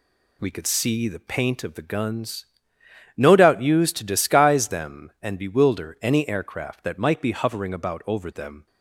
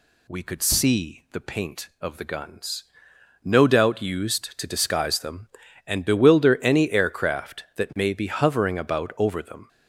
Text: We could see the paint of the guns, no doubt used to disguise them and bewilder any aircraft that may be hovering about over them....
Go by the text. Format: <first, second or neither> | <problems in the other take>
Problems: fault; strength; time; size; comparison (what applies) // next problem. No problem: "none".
second | says "might" for "may"; at 6.9 s